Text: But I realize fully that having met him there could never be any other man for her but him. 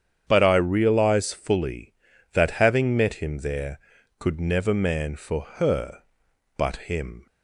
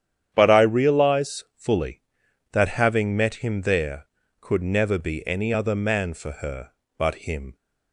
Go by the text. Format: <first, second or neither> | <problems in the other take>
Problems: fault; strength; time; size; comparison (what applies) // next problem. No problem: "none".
second | starts louder than the rest; strong; until 1.2 s; 8.5 dB; strong in the second // skips "be any other"; at 4.7 s // pauses between "for" and "her"; slight; at 5.4 s; 0.16 s long